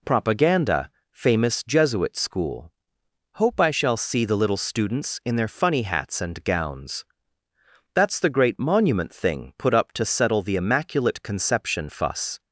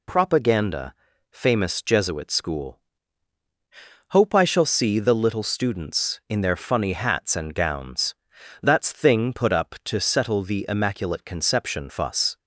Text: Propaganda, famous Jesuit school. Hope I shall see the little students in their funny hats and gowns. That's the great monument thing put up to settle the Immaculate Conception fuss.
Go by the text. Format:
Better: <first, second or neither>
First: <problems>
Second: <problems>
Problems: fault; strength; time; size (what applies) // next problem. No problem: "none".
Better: first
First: none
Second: skips "the great monument"; at 8.9 s